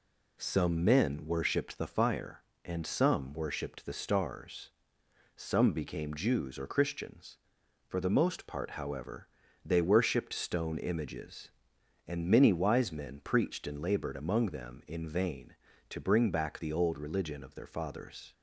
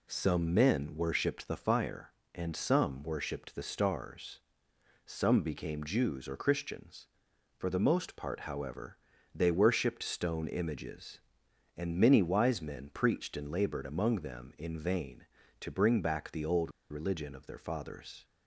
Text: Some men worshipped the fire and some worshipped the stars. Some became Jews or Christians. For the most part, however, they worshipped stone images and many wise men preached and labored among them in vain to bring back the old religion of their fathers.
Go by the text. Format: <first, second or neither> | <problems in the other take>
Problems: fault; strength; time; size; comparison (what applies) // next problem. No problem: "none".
first | pauses between "old" and "religion"; slight; at 16.7 s; 0.19 s long